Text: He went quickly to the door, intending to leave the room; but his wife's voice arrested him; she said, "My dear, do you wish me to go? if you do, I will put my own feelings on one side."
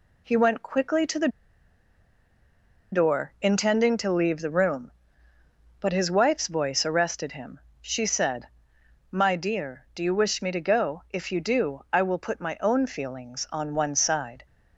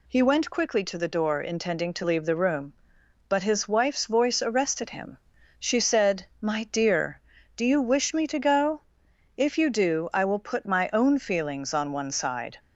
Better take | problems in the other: second | pauses between "the" and "door"; strong; at 1.2 s; 1.6 s long

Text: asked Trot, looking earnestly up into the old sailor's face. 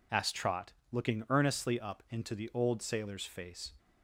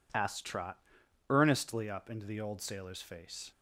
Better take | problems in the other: first | skips "looking"; at 1.0 s

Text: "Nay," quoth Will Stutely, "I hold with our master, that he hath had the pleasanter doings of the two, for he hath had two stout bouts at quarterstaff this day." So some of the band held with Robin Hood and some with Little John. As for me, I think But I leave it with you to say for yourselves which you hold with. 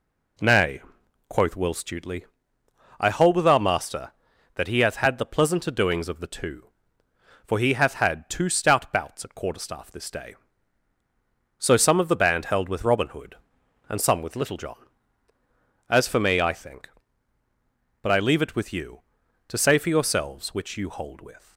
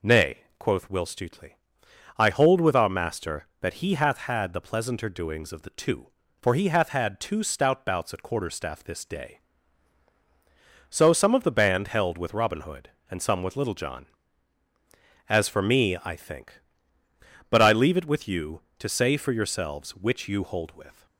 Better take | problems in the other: neither | none

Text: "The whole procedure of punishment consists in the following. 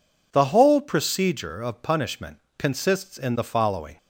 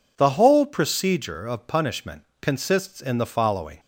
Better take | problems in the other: neither | pauses between "punishment" and "consists"; slight; the same in both

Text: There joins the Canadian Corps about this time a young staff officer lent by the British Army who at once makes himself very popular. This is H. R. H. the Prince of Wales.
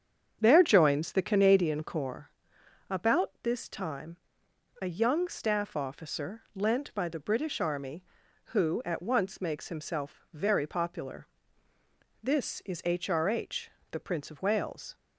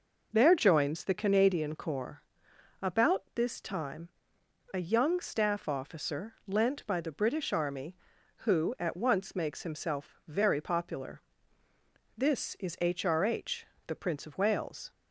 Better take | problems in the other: second | starts louder than the rest; strong; until 2.1 s; 7.5 dB // pauses between "Corps" and "about"; noticeable; at 2.2 s; 0.58 s long; noticeable in the second // pauses between "time" and "a"; noticeable; at 4.1 s; 0.64 s long; noticeable in the second // pauses between "officer" and "lent"; slight; at 6.3 s; 0.16 s long; slight in the second // pauses between "H" and "the"; slight; at 13.6 s; 0.22 s long; slight in the second

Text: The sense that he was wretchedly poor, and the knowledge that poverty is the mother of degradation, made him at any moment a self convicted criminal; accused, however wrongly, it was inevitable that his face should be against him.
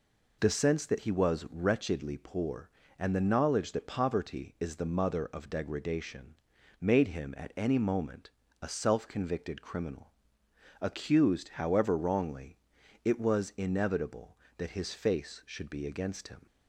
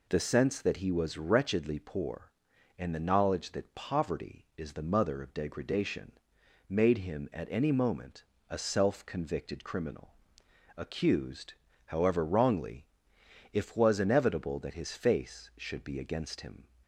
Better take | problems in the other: first | pauses between "moment" and "a"; slight; at 8.2 s; 0.24 s long; slight in the first // says "if" for "it"; at 13.5 s

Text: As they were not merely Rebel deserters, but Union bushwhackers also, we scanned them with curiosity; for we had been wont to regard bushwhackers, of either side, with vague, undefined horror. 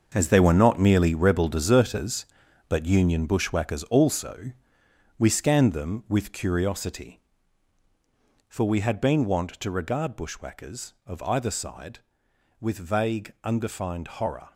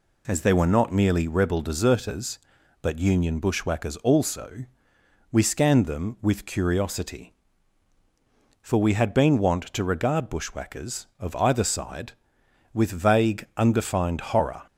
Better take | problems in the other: second | gets quieter; strong; throughout; 10.5 dB

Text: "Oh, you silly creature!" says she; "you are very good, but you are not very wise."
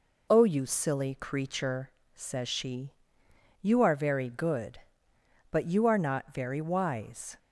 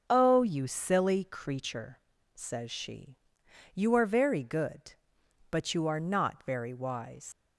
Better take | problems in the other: first | starts louder than the rest; until 1.0 s; 6.5 dB // leaves "wise" unfinished; at 7.3 s; 105 ms

